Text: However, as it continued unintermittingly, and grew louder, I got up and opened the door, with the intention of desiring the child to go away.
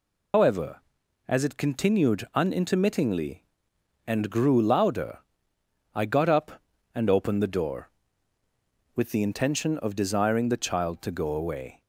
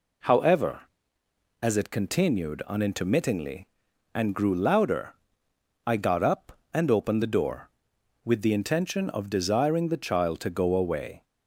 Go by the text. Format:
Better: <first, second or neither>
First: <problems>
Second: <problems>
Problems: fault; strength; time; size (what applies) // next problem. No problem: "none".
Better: second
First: loses the start of "However"; at 0.3 s; 145 ms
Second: none